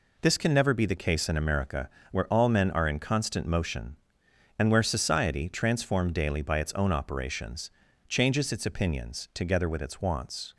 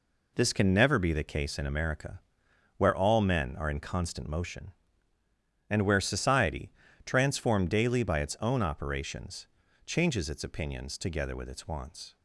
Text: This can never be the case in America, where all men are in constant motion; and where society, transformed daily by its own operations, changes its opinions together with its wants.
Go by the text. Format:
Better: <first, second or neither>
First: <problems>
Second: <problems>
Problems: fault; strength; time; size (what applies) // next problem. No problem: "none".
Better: neither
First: none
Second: none